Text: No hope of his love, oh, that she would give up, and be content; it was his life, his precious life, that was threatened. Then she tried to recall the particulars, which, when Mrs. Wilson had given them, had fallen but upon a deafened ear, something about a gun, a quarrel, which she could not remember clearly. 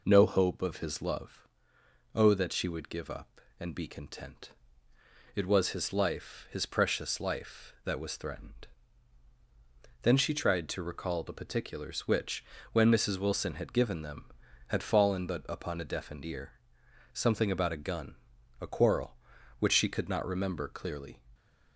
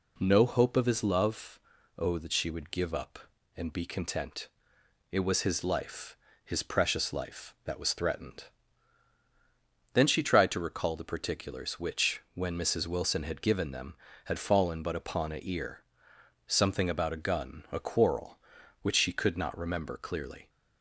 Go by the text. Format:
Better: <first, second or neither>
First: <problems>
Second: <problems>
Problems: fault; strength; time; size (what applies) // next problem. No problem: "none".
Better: first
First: none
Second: skips "deafened"; at 15.4 s